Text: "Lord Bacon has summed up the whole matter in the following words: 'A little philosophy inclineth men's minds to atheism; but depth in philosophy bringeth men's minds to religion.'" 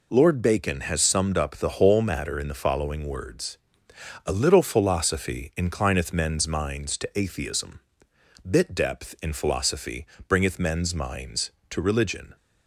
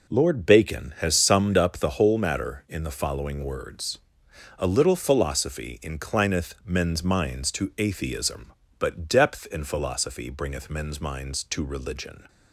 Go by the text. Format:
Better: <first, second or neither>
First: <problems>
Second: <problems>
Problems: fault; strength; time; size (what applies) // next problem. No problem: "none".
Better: second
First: says "bit" for "but"; at 8.4 s // pauses between "philosophy" and "bringeth"; slight; at 10.0 s; 0.22 s long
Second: none